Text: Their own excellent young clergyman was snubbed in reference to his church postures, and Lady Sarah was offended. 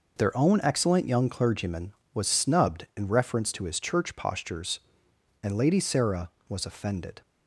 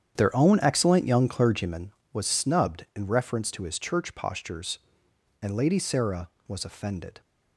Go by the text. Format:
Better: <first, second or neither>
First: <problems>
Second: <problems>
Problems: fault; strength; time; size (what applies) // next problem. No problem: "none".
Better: first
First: none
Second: starts louder than the rest; strong; until 1.7 s; 9 dB